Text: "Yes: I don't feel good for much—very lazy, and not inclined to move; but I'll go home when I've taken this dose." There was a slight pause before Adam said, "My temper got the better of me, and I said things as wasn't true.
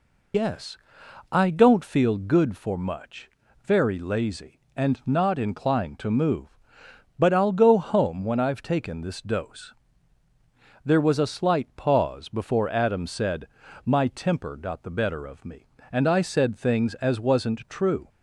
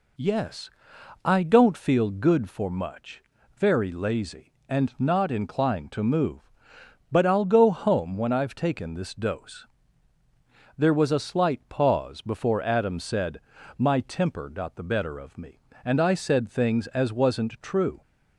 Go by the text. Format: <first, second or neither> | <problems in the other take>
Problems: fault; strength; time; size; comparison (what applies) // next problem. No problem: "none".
second | loses the start of "Yes"; at 0.3 s; 90 ms